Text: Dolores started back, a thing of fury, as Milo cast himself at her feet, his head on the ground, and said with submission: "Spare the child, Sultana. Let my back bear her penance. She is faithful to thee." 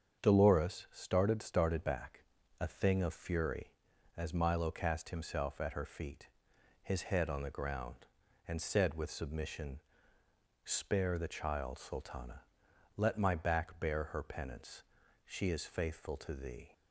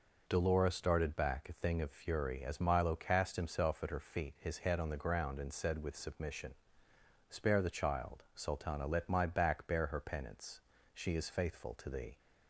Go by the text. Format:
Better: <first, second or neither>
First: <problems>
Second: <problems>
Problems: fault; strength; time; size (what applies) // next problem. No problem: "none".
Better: second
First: starts louder than the rest; strong; until 1.2 s; 7.5 dB // says "started" twice; at 1.4 s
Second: none